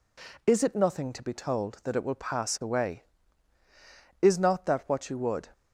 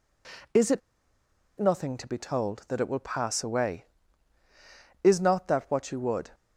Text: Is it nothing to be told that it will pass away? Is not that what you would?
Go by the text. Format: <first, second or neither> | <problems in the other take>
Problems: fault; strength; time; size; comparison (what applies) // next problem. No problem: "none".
first | pauses between "it" and "nothing"; noticeable; at 0.8 s; 0.78 s long